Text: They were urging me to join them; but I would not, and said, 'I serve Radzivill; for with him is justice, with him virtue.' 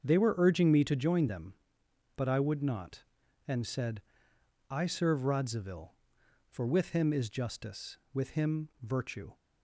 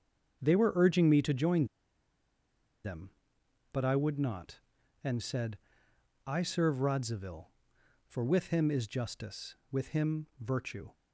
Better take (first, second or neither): first